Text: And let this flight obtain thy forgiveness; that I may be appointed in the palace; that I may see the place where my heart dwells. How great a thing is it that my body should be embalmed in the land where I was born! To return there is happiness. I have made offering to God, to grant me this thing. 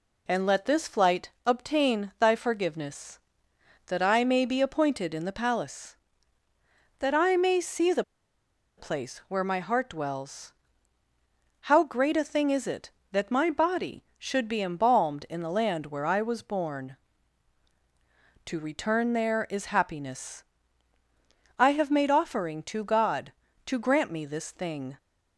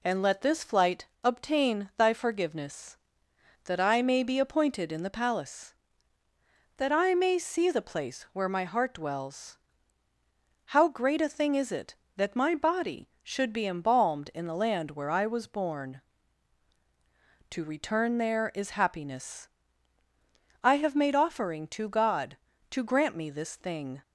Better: second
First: pauses between "flight" and "obtain"; slight; at 1.2 s; 0.16 s long // pauses between "the" and "place"; noticeable; at 8.0 s; 0.75 s long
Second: pauses between "flight" and "obtain"; slight; at 1.0 s; 0.17 s long

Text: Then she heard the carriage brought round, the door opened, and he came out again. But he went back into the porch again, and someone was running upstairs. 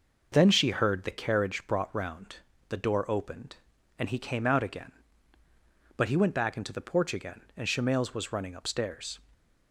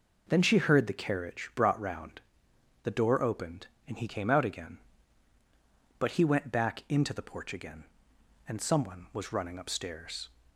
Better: second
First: says "shemales" for "someone"; at 7.6 s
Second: none

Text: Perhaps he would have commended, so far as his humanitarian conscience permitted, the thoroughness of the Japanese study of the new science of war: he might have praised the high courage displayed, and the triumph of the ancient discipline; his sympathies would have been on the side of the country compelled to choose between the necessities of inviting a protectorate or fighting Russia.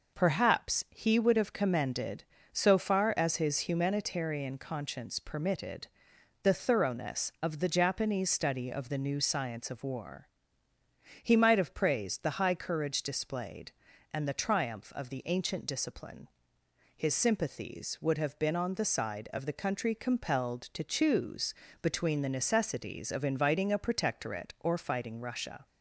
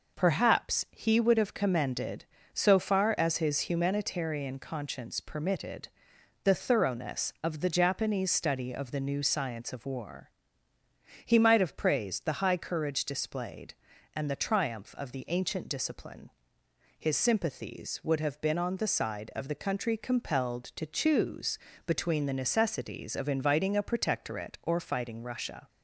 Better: neither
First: pauses between "choose" and "between"; slight; at 21.5 s; 0.28 s long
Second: pauses between "choose" and "between"; slight; at 21.5 s; 0.28 s long

